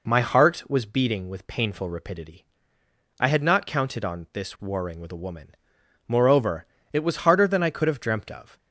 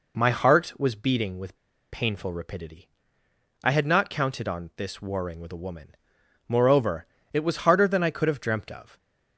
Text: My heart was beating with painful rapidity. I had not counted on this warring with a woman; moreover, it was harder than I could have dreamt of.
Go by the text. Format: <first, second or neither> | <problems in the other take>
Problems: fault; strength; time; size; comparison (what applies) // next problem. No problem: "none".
first | pauses between "with" and "painful"; slight; at 1.5 s; 0.34 s long